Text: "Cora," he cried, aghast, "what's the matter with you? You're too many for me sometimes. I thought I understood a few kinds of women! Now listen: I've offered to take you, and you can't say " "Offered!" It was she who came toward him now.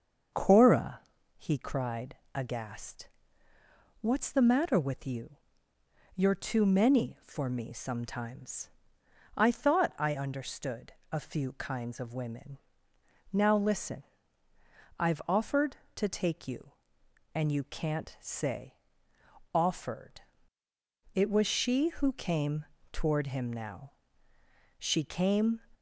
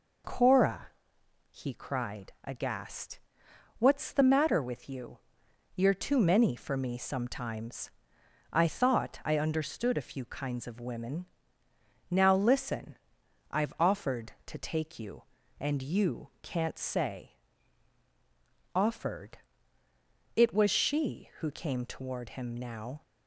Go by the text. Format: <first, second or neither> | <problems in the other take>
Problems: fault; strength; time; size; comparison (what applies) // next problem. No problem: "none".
second | starts louder than the rest; until 1.7 s; 6.5 dB // pauses between "understood" and "a"; slight; at 10.9 s; 0.18 s long // pauses between "came" and "toward"; slight; at 22.6 s; 0.26 s long // goes on to say "She came"; noticeable; from 24.7 s on; 0.82 s long